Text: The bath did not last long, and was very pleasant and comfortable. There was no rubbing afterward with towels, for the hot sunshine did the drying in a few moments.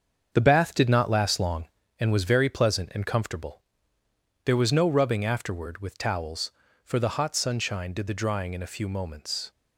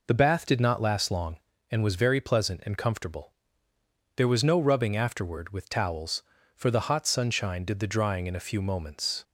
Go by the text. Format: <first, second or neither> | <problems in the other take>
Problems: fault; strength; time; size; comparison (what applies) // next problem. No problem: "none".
second | gets quieter; strong; throughout; 7.5 dB